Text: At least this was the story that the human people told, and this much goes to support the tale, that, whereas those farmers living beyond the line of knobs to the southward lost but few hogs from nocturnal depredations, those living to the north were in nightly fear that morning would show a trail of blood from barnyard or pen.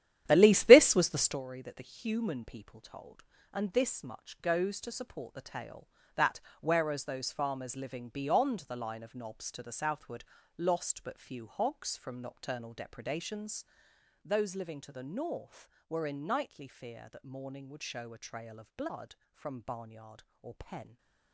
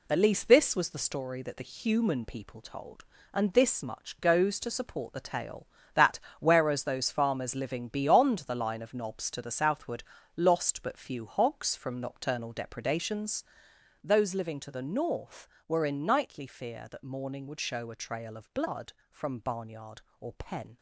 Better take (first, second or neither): second